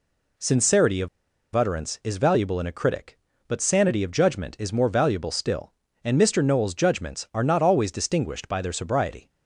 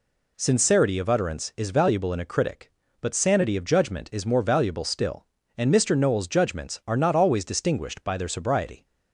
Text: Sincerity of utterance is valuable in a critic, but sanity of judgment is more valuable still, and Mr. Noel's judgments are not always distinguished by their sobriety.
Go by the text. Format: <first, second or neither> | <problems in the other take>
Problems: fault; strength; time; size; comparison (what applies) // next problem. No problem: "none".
second | pauses between "of" and "utterance"; noticeable; at 1.0 s; 0.46 s long